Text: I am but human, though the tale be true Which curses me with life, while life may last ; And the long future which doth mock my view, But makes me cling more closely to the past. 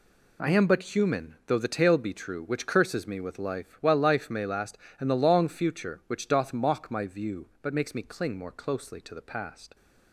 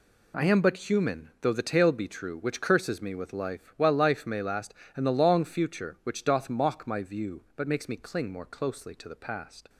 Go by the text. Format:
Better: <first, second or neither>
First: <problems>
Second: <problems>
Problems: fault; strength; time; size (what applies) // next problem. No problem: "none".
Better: neither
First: none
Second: none